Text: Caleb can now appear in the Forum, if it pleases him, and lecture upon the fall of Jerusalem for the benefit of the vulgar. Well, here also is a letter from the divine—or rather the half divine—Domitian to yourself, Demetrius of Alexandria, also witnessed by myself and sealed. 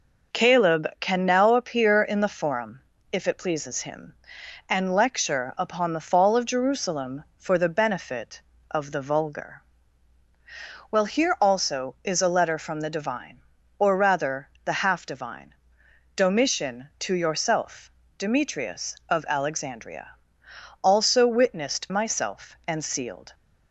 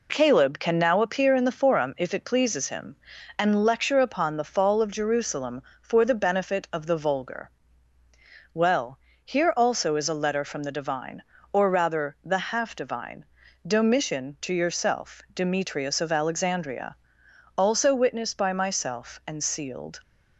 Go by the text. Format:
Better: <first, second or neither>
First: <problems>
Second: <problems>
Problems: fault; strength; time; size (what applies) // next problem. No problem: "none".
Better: second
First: skips "by"; at 21.8 s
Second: none